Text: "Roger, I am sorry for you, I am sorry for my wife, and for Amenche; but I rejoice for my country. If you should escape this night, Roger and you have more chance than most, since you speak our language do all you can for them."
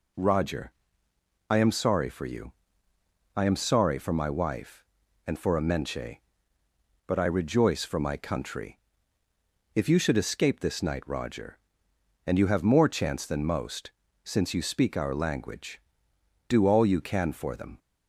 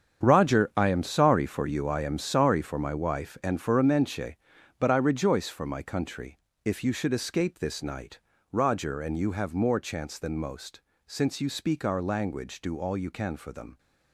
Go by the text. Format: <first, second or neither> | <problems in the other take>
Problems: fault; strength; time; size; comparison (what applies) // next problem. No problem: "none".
first | gets quieter; strong; throughout; 11.5 dB